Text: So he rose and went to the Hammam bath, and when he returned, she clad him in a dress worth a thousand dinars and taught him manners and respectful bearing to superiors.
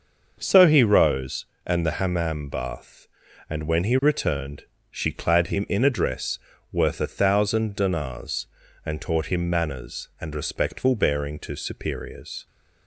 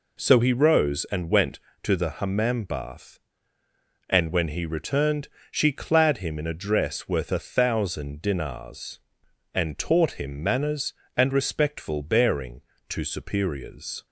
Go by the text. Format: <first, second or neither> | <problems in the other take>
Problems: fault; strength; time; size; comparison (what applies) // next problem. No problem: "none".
second | starts louder than the rest; until 1.3 s; 6 dB // skips "went to"; at 1.8 s // pauses between "dress" and "worth"; slight; at 6.3 s; 0.32 s long